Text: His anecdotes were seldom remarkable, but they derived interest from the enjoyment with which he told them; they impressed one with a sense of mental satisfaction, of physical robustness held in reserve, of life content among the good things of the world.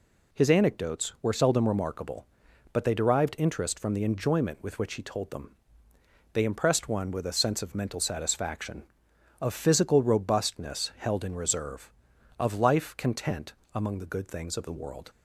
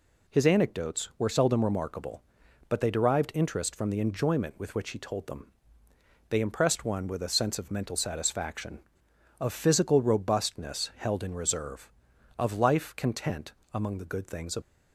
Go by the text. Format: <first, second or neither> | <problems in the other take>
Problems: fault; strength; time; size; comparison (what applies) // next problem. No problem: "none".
first | pauses between "content" and "among"; slight; at 13.5 s; 0.20 s long; slight in the first // stops before "the world"; at 14.6 s